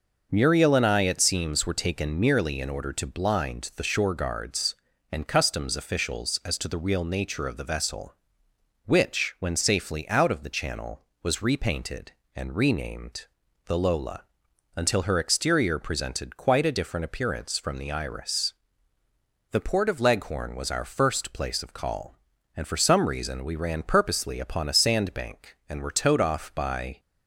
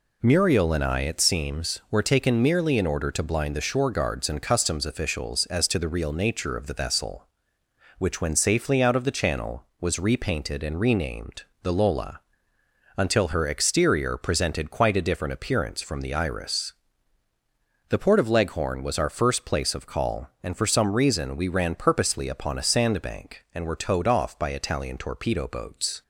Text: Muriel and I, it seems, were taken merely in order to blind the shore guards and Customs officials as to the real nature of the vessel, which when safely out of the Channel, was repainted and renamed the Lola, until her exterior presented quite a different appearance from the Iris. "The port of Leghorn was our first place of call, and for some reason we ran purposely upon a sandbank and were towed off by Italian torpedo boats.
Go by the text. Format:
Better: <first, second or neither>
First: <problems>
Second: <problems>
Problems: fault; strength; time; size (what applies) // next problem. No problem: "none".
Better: second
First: pauses between "renamed" and "the"; at 13.2 s; 0.40 s long // stops before "Italian torpedo boats"; at 26.9 s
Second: pauses between "renamed" and "the"; slight; at 11.4 s; 0.18 s long